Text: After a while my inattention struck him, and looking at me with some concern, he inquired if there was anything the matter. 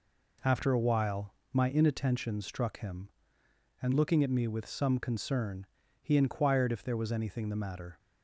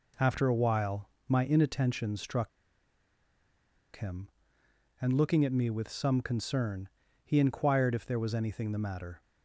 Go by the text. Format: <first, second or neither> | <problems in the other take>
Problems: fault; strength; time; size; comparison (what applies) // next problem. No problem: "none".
first | pauses between "while" and "my"; slight; at 1.0 s; 0.18 s long; slight in the first // pauses between "struck" and "him"; strong; at 2.4 s; 1.4 s long